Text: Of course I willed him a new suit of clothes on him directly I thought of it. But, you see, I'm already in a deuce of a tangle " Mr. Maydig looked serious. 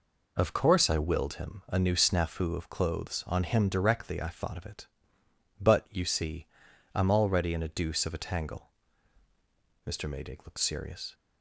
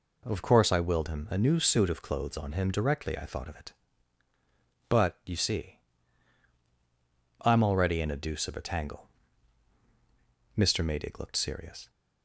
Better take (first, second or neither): second